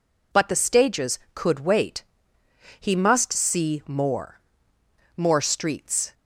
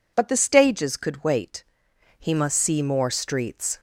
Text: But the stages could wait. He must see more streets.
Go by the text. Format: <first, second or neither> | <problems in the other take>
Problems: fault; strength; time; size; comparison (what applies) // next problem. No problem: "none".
second | says "more" twice; at 5.1 s